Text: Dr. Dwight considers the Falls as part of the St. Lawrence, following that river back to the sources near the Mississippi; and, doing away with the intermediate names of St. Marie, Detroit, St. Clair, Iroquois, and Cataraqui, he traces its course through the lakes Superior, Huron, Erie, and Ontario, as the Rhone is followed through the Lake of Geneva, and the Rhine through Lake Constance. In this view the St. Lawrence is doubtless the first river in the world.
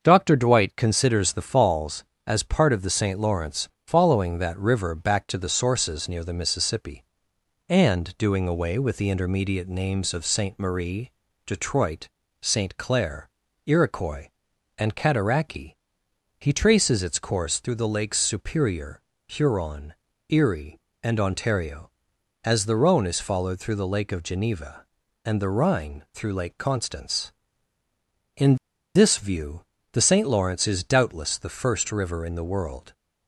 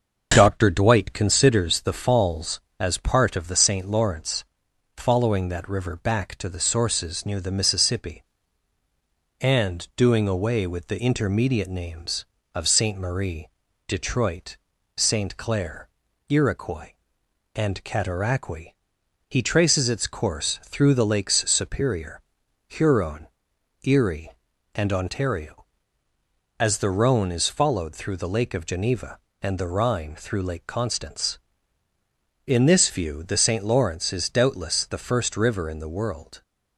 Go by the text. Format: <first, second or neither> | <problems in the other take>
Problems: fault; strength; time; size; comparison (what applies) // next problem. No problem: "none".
second | starts louder than the rest; until 1.0 s; 6.5 dB // pauses between "In" and "this"; at 28.5 s; 0.40 s long // pauses between "view" and "the"; slight; at 29.6 s; 0.28 s long